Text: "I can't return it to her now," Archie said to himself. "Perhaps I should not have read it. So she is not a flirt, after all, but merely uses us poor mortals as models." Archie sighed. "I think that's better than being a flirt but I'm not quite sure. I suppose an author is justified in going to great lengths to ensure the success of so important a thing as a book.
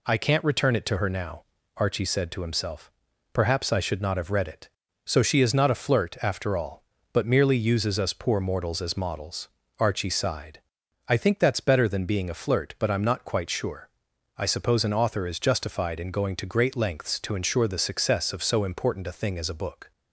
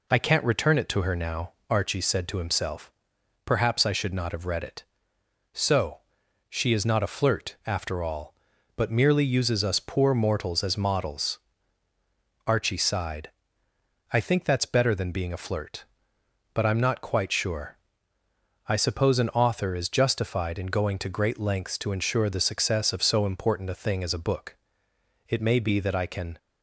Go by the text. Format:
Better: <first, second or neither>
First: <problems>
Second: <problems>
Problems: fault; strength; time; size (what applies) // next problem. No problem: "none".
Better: first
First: none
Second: pauses between "So" and "she"; noticeable; at 5.9 s; 0.48 s long // goes on to say "It may be that I can"; noticeable; from 25.2 s on; 1.1 s long